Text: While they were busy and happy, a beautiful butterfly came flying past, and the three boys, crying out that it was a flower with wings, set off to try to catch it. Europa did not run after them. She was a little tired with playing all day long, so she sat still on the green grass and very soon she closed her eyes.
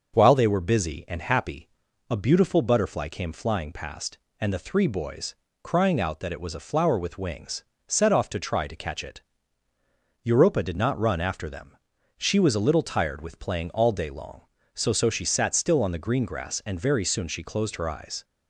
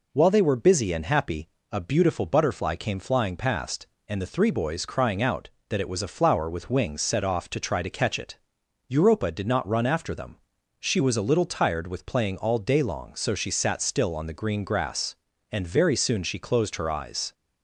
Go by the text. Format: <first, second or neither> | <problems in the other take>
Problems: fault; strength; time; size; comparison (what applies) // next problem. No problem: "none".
second | starts louder than the rest; until 1.1 s; 6.5 dB // says "so" twice; at 14.9 s